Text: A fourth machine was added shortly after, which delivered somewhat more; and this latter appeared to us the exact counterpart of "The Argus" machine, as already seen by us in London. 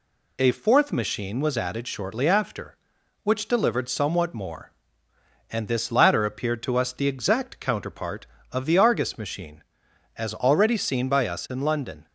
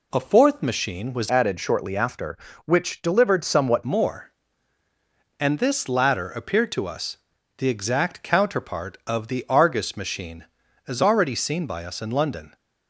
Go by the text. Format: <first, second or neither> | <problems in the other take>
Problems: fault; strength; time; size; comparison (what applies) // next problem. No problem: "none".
first | changes voice from "added" to "somewhat"; from 1.2 to 3.8 s; 2.6 s long // pauses between "us" and "the"; at 7.1 s; 0.40 s long